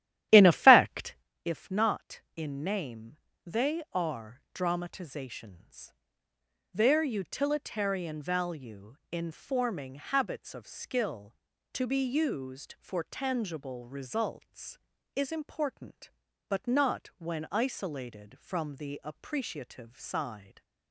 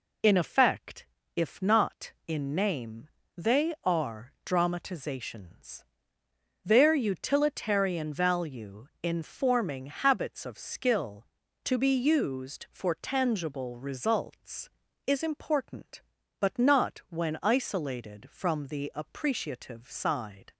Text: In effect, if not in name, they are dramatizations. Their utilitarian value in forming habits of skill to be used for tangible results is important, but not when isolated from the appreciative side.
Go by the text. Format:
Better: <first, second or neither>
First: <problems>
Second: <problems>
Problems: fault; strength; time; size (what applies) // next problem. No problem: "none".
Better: second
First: starts louder than the rest; strong; until 1.3 s; 13 dB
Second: none